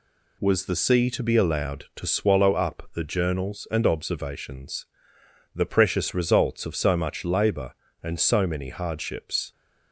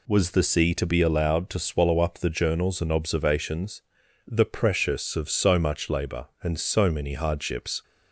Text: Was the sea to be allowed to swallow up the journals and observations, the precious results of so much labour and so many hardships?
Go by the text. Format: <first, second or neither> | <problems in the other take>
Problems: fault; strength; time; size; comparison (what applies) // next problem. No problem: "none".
first | skips "results"; at 5.1 s